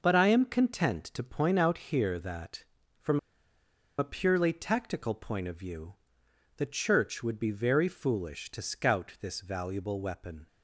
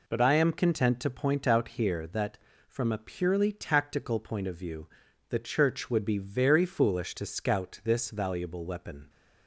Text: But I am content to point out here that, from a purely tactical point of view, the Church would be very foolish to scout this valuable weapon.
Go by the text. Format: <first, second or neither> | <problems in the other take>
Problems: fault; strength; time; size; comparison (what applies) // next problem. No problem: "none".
second | pauses between "from" and "a"; noticeable; at 3.1 s; 0.79 s long